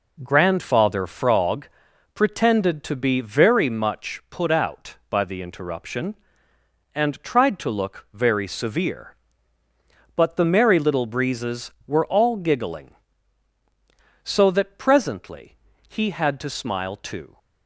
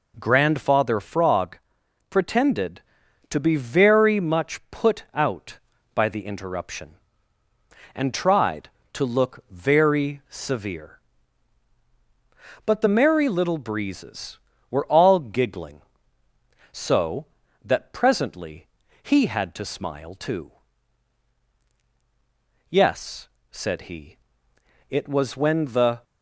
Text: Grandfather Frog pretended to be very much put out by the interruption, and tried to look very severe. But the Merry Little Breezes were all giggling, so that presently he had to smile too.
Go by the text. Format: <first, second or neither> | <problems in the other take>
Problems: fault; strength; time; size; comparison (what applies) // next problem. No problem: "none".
first | pauses between "Frog" and "pretended"; noticeable; at 1.5 s; 0.52 s long; also in the first // pauses between "presently" and "he"; at 18.6 s; 0.38 s long; slight in the first // goes on to say "Yes said he it was when the"; strong; from 22.6 s on; 3.3 s long